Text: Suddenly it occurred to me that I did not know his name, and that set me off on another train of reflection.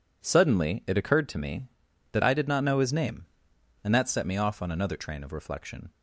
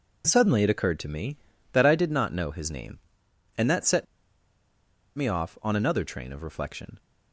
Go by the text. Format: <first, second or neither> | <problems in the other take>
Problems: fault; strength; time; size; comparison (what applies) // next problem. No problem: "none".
first | pauses between "set" and "me"; at 4.0 s; 1.1 s long